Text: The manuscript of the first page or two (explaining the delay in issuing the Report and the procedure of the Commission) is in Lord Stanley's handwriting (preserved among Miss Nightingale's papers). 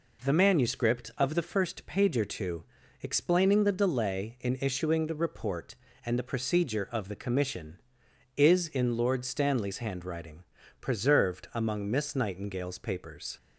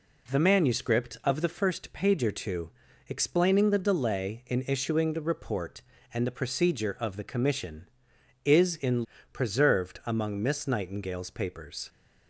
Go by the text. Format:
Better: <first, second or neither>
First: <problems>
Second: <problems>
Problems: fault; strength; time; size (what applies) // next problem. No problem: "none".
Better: first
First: none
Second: skips "Lord Stanley's handwriting"; at 9.1 s